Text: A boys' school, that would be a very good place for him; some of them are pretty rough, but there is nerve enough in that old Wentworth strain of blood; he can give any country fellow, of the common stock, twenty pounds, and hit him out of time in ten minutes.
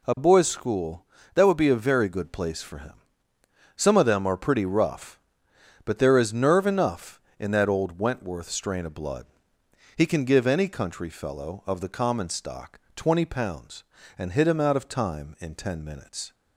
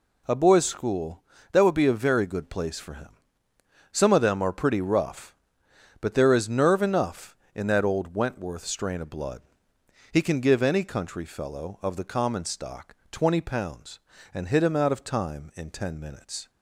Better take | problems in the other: neither | none

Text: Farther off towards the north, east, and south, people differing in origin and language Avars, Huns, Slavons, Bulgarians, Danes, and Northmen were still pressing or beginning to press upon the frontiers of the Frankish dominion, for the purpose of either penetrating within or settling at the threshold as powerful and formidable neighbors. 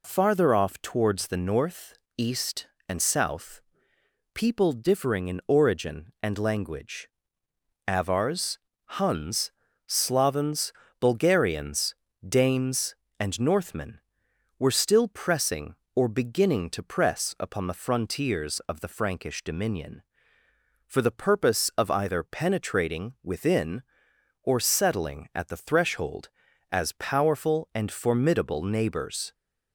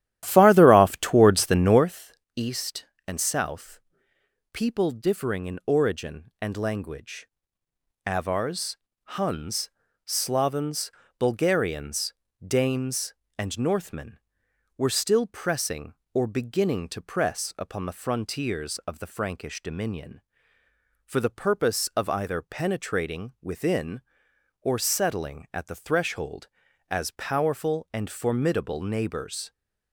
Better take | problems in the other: first | starts louder than the rest; strong; until 2.0 s; 12.5 dB // pauses between "language" and "Avars"; noticeable; at 7.2 s; 0.76 s long; noticeable in the first

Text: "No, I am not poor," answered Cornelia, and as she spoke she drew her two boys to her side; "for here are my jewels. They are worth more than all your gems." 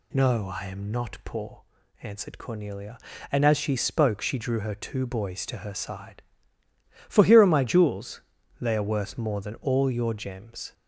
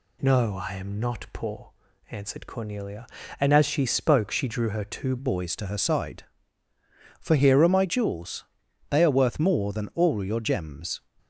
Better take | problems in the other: first | changes voice at "boys"; from 5.1 s on; 5.9 s long

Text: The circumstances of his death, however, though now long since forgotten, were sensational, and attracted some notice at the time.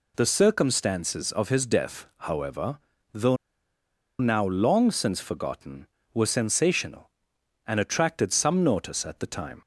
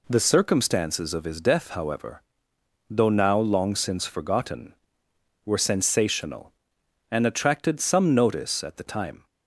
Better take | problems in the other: second | pauses between "though" and "now"; noticeable; at 3.3 s; 0.84 s long

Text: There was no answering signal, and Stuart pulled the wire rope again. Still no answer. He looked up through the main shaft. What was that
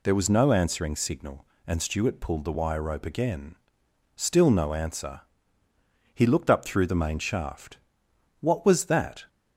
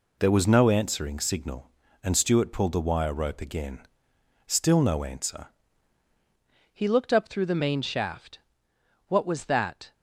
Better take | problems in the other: first | changes voice at "He"; from 6.7 s on; 3.2 s long

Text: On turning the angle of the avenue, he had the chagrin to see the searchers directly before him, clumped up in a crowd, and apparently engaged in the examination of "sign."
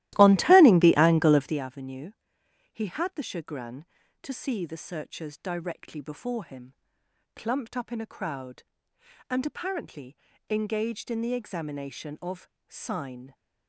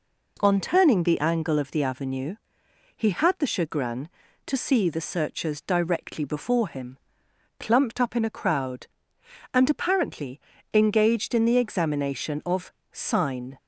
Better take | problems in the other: second | starts louder than the rest; strong; until 1.6 s; 15.5 dB // pauses between "apparently" and "engaged"; slight; at 10.1 s; 0.32 s long; slight in the second // pauses between "of" and "sign"; slight; at 12.4 s; 0.20 s long; slight in the second

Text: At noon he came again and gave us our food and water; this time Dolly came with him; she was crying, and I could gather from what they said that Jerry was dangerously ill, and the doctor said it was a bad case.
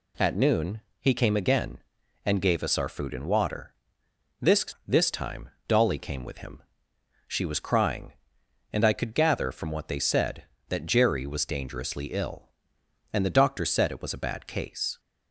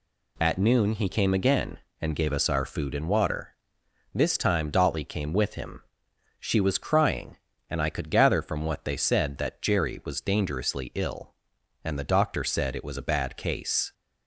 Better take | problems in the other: second | pauses between "noon" and "he"; slight; at 0.7 s; 0.20 s long // says "this" twice; at 4.8 s // pauses between "time" and "Dolly"; slight; at 5.4 s; 0.18 s long

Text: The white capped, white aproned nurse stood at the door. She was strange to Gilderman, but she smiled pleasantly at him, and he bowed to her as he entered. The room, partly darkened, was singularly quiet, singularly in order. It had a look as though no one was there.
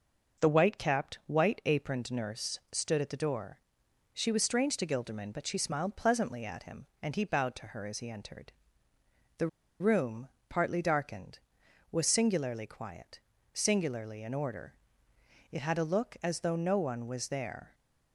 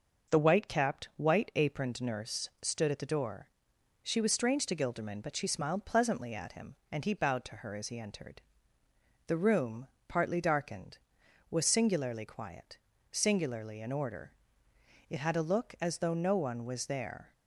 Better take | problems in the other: second | pauses between "The" and "room"; slight; at 9.4 s; 0.32 s long

